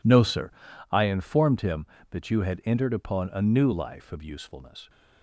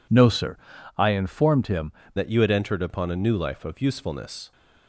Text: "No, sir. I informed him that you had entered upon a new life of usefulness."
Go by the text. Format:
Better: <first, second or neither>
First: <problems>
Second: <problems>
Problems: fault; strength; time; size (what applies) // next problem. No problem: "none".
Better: first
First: none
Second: changes voice at "that"; from 2.1 s on; 2.4 s long